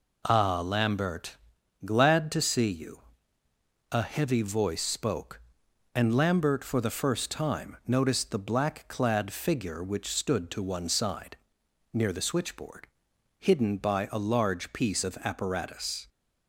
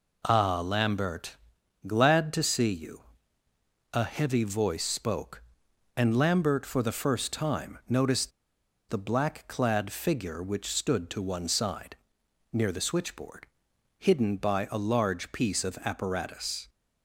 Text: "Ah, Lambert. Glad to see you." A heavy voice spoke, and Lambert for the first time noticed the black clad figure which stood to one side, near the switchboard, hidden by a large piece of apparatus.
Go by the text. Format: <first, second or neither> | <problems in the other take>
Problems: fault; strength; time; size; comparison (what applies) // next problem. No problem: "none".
first | pauses between "noticed" and "the"; noticeable; at 8.3 s; 0.57 s long